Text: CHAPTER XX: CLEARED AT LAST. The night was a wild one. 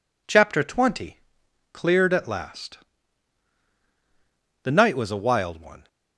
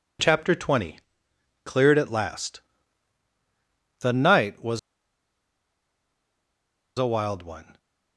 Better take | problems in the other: first | pauses between "was" and "a"; strong; at 4.7 s; 2.2 s long

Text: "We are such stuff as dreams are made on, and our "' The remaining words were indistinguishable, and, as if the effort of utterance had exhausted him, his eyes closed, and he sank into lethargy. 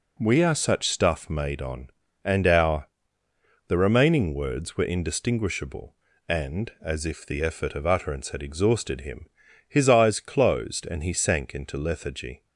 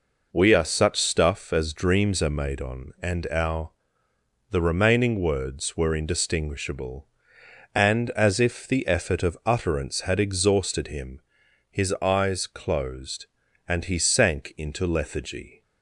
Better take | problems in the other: second | skips "as dreams are"; at 1.2 s

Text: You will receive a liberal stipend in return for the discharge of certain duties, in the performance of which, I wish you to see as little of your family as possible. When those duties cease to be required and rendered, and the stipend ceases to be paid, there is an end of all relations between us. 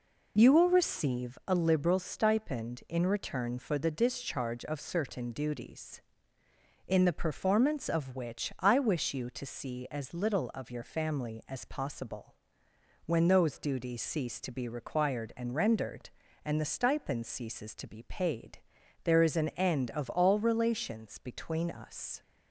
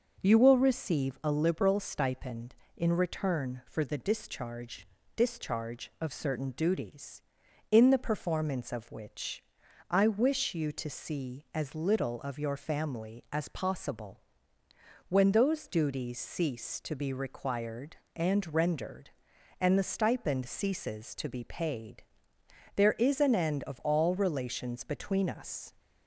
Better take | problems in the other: first | starts louder than the rest; noticeable; until 1.2 s; 6 dB // says "discharge" twice; at 5.1 s

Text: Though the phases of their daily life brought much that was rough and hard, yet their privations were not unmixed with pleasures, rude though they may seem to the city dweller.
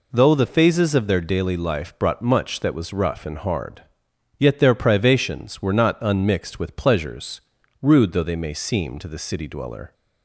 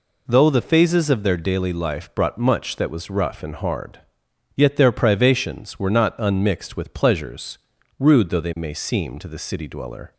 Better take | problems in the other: neither | none

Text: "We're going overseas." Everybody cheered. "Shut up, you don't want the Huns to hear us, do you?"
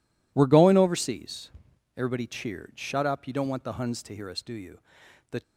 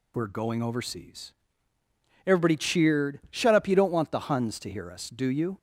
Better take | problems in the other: second | goes on to say "The"; slight; from 5.3 s on; 0.12 s long

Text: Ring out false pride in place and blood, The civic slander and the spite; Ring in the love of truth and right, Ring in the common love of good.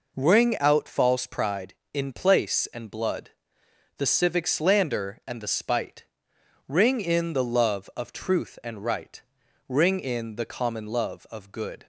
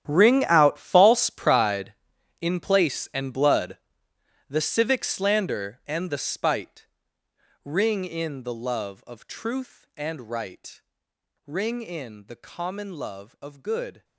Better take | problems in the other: first | gets quieter; strong; throughout; 16 dB

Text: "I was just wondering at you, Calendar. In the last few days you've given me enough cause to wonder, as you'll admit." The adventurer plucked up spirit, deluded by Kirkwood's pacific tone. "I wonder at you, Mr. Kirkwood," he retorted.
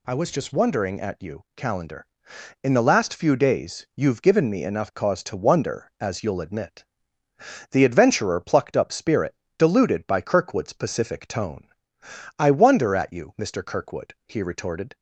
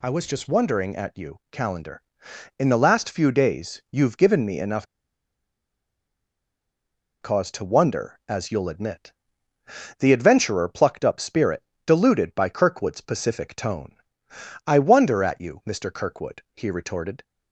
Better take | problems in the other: first | pauses between "enough" and "cause"; strong; at 4.8 s; 2.3 s long

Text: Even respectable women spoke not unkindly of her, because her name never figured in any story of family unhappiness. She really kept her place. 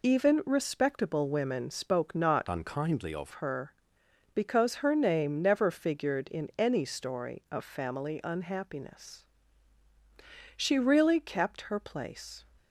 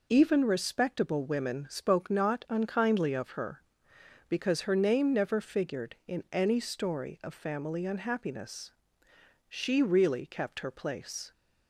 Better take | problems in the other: second | changes voice from "unkindly" to "of"; from 2.4 to 3.3 s; 0.9 s long

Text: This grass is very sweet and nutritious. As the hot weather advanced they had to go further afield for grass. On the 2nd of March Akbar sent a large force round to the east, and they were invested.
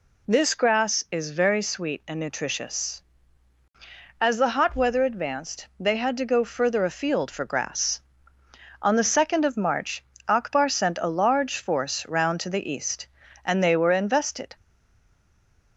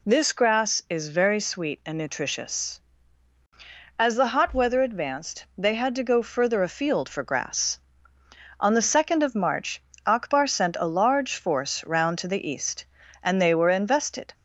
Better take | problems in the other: second | pauses between "March" and "Akbar"; slight; at 10.0 s; 0.24 s long; slight in the second // stays silent after the last word; noticeable; from 14.5 s on; 1.2 s long

